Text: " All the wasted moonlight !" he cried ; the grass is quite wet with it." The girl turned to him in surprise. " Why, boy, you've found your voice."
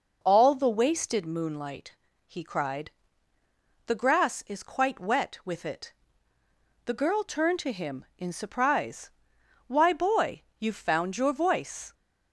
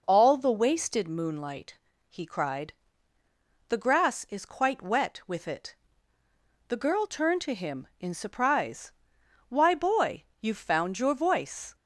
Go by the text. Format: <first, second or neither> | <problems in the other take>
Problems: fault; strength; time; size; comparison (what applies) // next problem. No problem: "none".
neither | none